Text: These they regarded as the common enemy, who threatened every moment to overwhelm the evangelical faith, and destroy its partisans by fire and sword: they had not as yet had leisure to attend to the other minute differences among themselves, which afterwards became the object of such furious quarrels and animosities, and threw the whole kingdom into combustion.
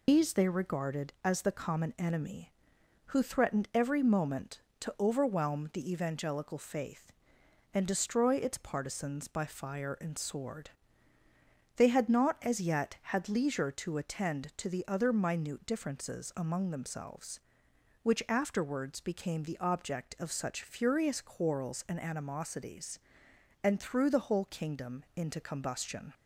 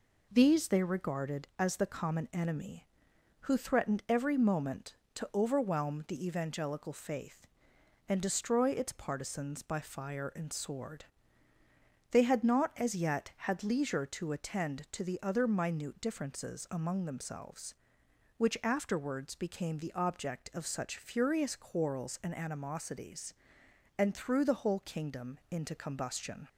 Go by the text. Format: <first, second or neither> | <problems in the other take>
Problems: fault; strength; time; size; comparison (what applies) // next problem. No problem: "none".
second | loses the start of "These"; at 0.0 s; 130 ms